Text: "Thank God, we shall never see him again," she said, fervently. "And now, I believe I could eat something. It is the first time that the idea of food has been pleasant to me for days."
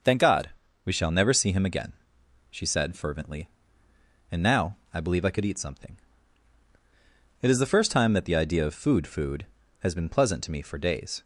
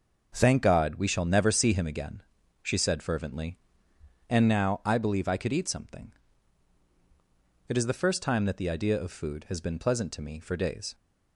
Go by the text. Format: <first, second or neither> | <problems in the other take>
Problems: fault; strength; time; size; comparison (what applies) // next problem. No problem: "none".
second | starts louder than the rest; noticeable; until 1.4 s; 6 dB // says "food" twice; at 9.0 s